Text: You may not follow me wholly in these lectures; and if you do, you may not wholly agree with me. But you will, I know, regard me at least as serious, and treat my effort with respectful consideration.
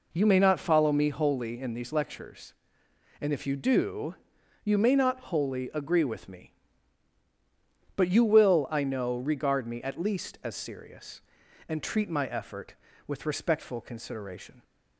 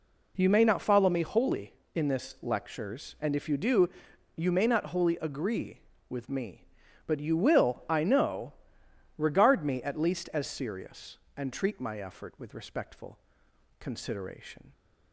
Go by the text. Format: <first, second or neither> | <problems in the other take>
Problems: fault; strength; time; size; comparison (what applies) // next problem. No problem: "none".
first | says "this" for "these"; at 2.0 s // pauses between "respectful" and "consideration"; noticeable; at 13.1 s; 0.62 s long